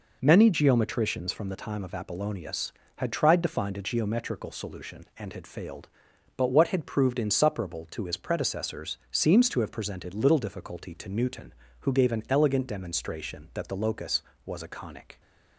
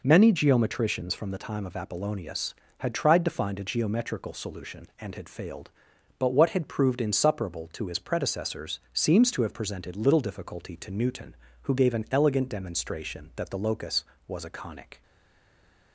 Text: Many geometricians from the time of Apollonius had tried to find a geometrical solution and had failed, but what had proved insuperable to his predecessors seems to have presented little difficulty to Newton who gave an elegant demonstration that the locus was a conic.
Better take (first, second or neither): first